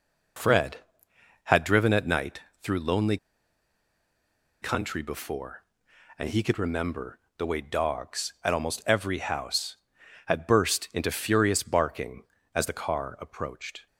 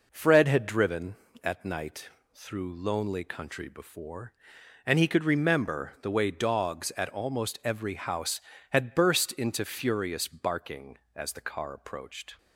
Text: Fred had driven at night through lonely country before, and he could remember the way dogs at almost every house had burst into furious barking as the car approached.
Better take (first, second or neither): second